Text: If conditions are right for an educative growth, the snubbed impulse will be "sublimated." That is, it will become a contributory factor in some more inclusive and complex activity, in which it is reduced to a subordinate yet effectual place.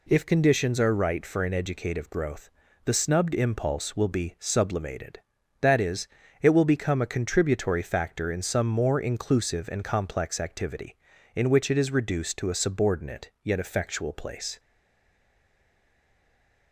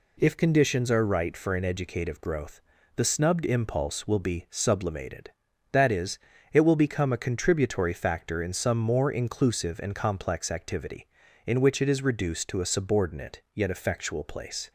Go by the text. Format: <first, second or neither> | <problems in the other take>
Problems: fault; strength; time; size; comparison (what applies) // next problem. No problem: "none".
second | stays silent after the last word; from 14.5 s on; 2.2 s long